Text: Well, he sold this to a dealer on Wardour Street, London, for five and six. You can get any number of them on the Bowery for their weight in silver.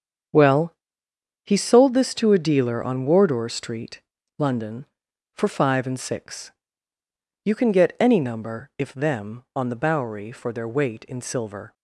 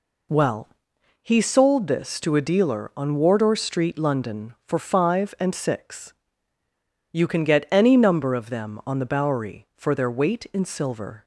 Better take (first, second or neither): second